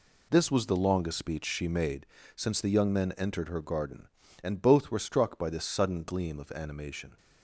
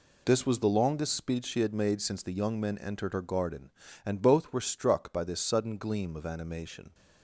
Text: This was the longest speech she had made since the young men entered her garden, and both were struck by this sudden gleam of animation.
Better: second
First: skips "had"; at 1.6 s // pauses between "made" and "since"; slight; at 2.0 s; 0.30 s long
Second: none

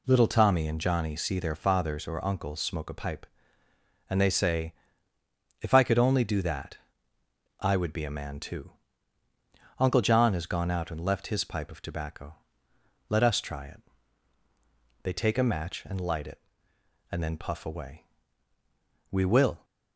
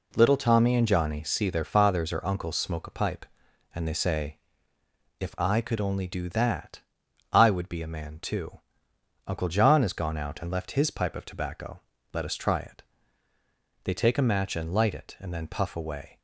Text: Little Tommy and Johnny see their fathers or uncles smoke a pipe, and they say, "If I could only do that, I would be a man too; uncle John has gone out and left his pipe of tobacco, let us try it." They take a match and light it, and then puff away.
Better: second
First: goes on to say "We will"; from 19.1 s on; 0.54 s long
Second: none

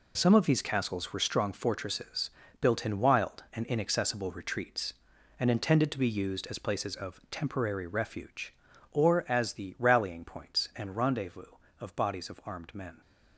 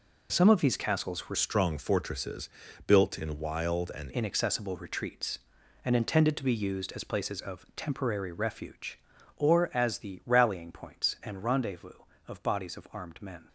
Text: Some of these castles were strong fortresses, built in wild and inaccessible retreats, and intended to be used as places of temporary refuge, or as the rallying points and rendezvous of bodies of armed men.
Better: first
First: none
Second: changes voice from "strong" to "and"; from 1.3 to 4.0 s; 2.7 s long

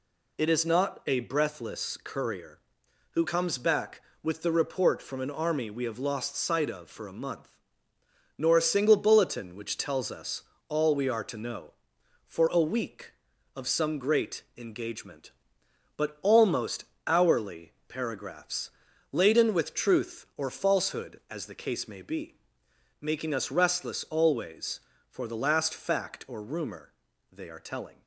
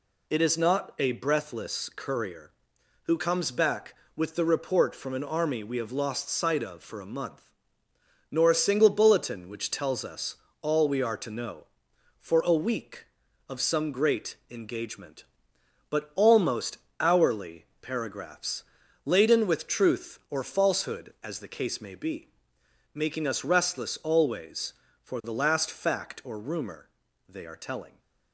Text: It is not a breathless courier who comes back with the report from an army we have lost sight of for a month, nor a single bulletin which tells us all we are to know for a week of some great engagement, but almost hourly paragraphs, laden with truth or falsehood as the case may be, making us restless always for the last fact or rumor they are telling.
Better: neither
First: pauses between "us" and "all"; slight; at 10.4 s; 0.28 s long // pauses between "great" and "engagement"; slight; at 14.4 s; 0.16 s long // pauses between "almost" and "hourly"; slight; at 16.8 s; 0.20 s long // pauses between "hourly" and "paragraphs"; slight; at 17.7 s; 0.16 s long // pauses between "rumor" and "they"; at 26.9 s; 0.40 s long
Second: pauses between "us" and "all"; slight; at 10.3 s; 0.28 s long // pauses between "great" and "engagement"; slight; at 14.3 s; 0.16 s long // pauses between "almost" and "hourly"; slight; at 16.7 s; 0.20 s long // pauses between "hourly" and "paragraphs"; slight; at 17.6 s; 0.16 s long // pauses between "rumor" and "they"; at 26.8 s; 0.40 s long

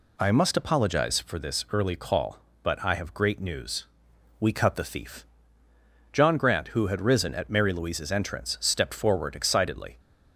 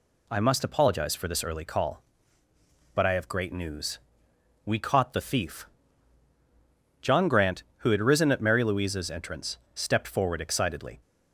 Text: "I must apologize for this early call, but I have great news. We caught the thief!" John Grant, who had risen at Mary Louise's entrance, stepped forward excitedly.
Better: second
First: says "cut" for "caught"; at 4.5 s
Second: none

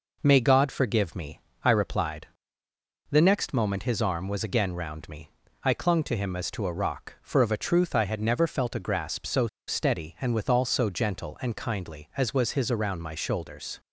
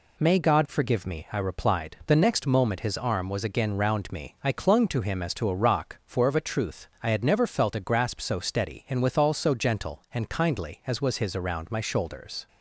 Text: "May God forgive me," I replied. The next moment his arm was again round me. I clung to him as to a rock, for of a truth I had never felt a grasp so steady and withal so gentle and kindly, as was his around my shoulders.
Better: second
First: pauses between "so" and "steady"; slight; at 9.4 s; 0.20 s long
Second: none

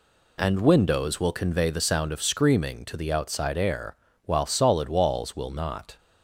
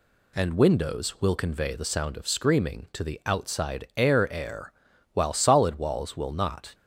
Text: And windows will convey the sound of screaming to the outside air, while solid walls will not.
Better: first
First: none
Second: says "air" twice; at 4.3 s

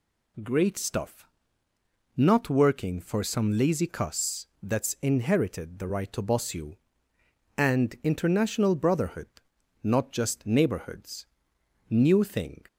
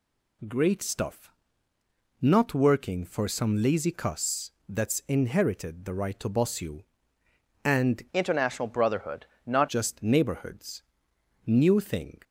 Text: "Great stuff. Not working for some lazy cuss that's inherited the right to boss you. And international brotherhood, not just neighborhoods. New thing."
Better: first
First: none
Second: pauses between "cuss" and "that's"; slight; at 4.5 s; 0.16 s long // changes voice from "international" to "not"; from 8.1 to 9.6 s; 1.5 s long

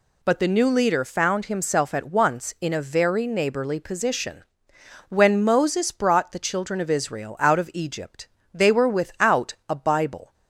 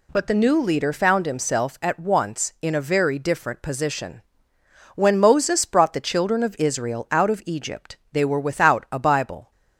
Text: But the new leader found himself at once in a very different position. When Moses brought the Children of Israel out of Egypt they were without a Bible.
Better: second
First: says "neighborly" for "different"; at 3.2 s // pauses between "Egypt" and "they"; slight; at 8.2 s; 0.26 s long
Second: none

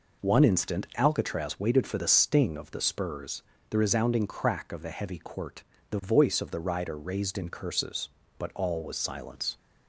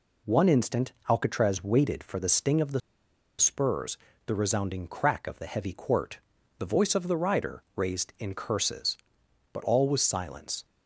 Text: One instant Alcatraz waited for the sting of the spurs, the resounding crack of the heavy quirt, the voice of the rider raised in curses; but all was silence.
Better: first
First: none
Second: pauses between "the" and "spurs"; noticeable; at 2.8 s; 0.58 s long

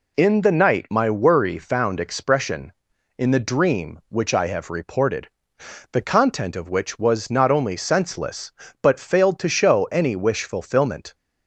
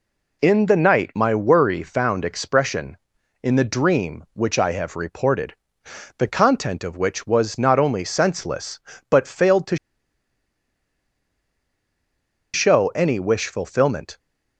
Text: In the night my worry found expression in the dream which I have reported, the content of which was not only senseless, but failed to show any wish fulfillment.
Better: first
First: none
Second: pauses between "to" and "show"; strong; at 9.7 s; 2.7 s long

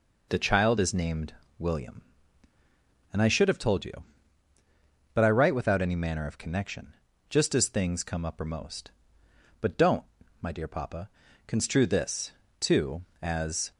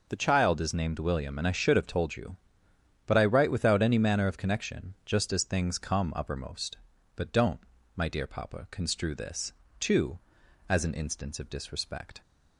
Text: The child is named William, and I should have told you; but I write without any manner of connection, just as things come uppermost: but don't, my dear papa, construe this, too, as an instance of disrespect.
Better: second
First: pauses between "named" and "William"; slight; at 1.3 s; 0.26 s long // stops before "an instance of disrespect"; at 13.7 s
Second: none

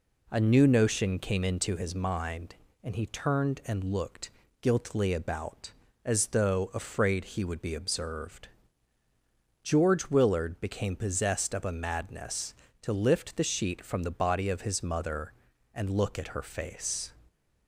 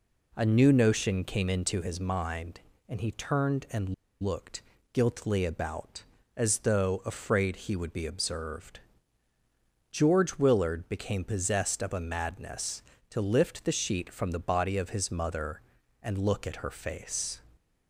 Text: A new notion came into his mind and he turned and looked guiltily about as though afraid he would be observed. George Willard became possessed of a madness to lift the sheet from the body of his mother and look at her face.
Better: first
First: pauses between "looked" and "guiltily"; slight; at 4.2 s; 0.30 s long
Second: pauses between "and" and "looked"; slight; at 3.9 s; 0.29 s long // pauses between "looked" and "guiltily"; slight; at 4.6 s; 0.30 s long

